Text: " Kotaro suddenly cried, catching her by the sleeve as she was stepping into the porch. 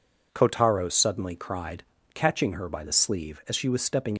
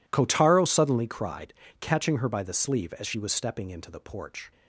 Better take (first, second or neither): second